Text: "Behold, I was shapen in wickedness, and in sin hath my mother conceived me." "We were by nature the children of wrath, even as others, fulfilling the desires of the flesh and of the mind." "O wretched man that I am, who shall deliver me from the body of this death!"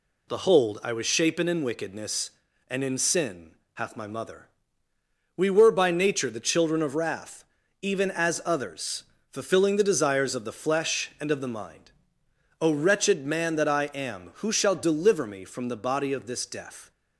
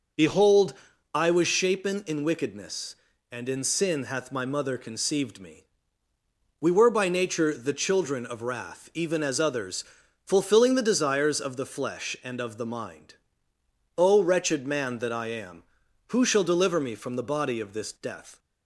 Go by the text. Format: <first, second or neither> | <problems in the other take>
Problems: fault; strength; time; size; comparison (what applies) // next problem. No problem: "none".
second | pauses between "sin" and "hath"; slight; at 3.5 s; 0.20 s long // skips "conceived me"; at 4.9 s